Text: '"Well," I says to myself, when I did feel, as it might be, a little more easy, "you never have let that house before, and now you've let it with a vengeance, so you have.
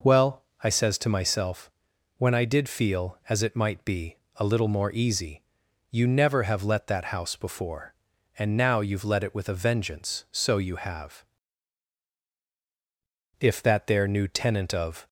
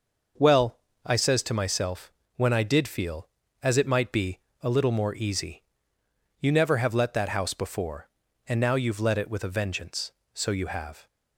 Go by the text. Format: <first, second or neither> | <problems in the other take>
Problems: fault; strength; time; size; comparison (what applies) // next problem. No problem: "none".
second | goes on to say "If that there new tenant of"; strong; from 13.3 s on; 1.6 s long